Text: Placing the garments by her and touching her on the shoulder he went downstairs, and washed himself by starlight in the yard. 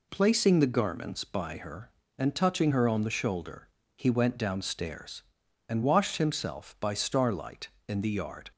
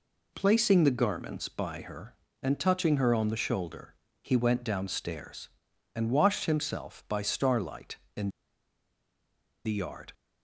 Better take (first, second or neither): first